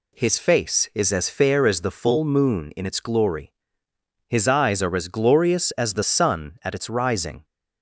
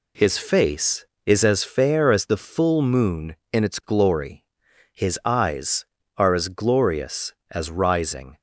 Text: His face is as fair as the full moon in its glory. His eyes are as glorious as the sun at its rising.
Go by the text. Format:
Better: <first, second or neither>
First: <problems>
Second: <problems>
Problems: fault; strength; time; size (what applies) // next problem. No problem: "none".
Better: first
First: none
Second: skips "the sun at its"; at 7.7 s